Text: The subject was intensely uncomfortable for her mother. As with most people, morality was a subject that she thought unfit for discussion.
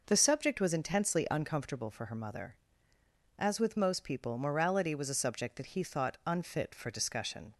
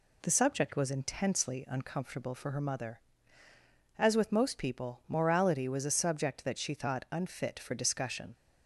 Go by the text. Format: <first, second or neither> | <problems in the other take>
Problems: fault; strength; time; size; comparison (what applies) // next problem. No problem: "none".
second | says "he" for "she"; at 5.7 s